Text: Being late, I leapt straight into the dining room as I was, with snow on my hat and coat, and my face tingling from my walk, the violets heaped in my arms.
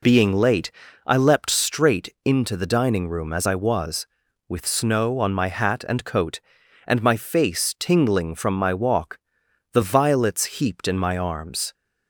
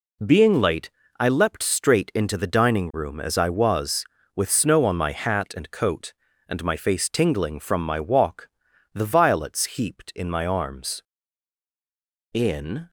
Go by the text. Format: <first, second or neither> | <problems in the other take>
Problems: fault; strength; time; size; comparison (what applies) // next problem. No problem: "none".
first | goes on to say "In"; from 12.3 s on; 0.56 s long